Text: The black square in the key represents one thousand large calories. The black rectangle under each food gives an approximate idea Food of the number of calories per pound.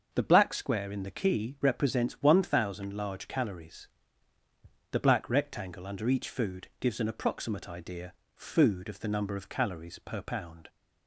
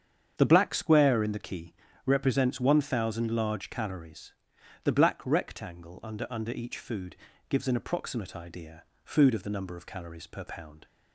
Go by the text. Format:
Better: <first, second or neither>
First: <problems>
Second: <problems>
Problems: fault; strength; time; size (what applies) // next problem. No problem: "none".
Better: first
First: starts louder than the rest; until 1.1 s; 6.5 dB // pauses between "idea" and "Food"; slight; at 8.1 s; 0.24 s long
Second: starts louder than the rest; strong; until 1.3 s; 8 dB // pauses between "key" and "represents"; slight; at 1.7 s; 0.32 s long // says "under" twice; at 6.3 s // pauses between "food" and "gives"; slight; at 7.1 s; 0.34 s long // pauses between "idea" and "Food"; slight; at 8.8 s; 0.20 s long